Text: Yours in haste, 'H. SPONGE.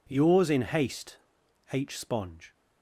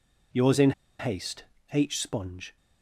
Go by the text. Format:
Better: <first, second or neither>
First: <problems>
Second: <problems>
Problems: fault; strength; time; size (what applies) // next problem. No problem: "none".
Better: first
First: none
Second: pauses between "in" and "haste"; slight; at 0.7 s; 0.28 s long